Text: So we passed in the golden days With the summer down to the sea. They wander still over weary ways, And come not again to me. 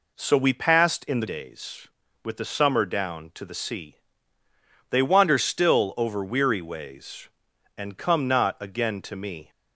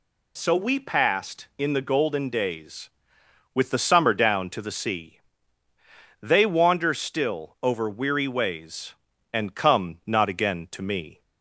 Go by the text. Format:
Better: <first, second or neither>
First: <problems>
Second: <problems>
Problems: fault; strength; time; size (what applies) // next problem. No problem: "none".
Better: second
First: skips "golden"; at 1.2 s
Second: none